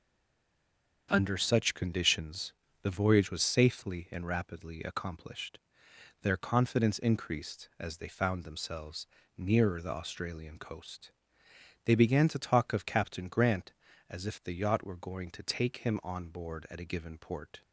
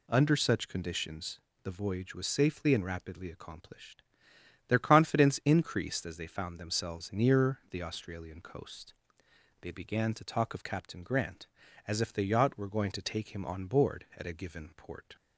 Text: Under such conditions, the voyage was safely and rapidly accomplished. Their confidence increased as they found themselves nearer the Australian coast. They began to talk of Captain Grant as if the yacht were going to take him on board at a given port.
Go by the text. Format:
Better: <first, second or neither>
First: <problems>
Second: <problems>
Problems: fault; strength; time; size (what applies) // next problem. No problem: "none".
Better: second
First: stays silent before the first word; until 1.0 s; 1.0 s long // starts louder than the rest; until 2.1 s; 7 dB // pauses between "themselves" and "nearer"; slight; at 9.0 s; 0.28 s long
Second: none